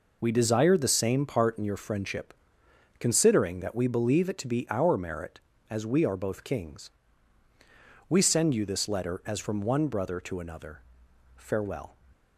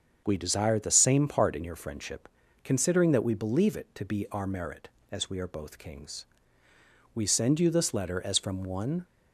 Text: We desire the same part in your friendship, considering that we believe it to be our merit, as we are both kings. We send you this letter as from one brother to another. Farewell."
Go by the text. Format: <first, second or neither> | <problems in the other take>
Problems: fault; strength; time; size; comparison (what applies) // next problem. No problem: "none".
first | starts louder than the rest; until 1.2 s; 7 dB // stops before "brother to another Farewell"; at 9.0 s